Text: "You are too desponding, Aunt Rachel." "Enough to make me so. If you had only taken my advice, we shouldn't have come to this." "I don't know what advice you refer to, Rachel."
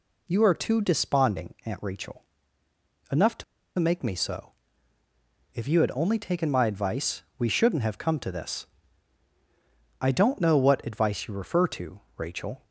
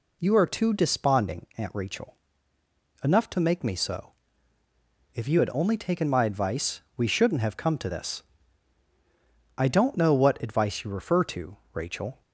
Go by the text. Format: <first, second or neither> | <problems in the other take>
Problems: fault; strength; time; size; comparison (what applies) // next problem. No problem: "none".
second | pauses between "to" and "make"; slight; at 3.4 s; 0.34 s long